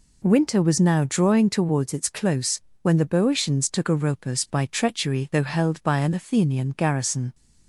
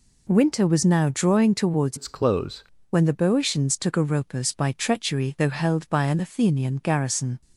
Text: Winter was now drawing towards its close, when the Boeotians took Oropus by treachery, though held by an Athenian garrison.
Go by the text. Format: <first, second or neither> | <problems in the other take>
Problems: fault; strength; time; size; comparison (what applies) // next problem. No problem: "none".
first | changes voice from "its" to "close"; from 1.9 to 2.6 s; 0.7 s long